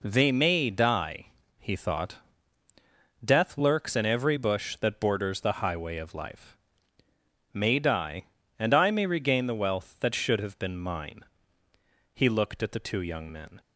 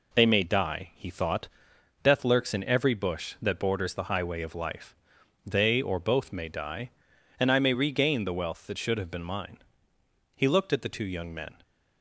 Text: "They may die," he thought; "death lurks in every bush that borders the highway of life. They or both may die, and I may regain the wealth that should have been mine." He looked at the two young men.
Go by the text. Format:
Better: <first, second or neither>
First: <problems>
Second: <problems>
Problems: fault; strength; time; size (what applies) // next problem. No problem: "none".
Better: second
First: skips "They or both"; at 7.0 s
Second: none